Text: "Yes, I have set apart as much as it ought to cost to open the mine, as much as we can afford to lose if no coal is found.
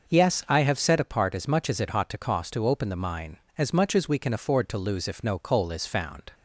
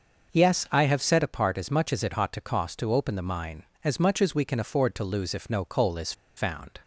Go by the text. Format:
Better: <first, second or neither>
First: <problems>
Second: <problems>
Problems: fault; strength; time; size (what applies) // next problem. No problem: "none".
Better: first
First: starts louder than the rest; noticeable; until 1.1 s; 6 dB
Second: starts louder than the rest; noticeable; until 1.3 s; 6 dB // pauses between "is" and "found"; slight; at 6.1 s; 0.24 s long